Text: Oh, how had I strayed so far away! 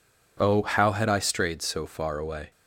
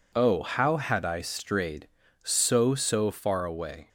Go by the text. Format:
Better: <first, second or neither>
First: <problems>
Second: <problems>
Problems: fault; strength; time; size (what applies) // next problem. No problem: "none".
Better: first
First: none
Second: says "so" twice; at 2.7 s